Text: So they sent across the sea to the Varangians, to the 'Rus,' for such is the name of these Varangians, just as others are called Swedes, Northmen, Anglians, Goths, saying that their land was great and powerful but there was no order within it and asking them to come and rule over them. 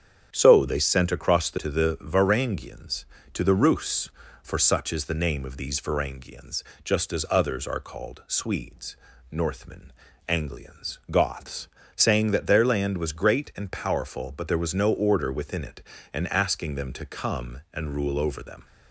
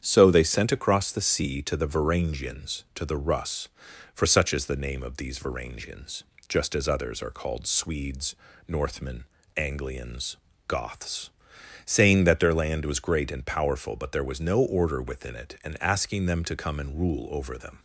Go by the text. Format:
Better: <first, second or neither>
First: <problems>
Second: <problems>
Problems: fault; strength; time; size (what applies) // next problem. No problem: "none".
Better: second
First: starts louder than the rest; strong; until 1.3 s; 8 dB // skips "sea"; at 1.5 s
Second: starts louder than the rest; strong; until 1.0 s; 8.5 dB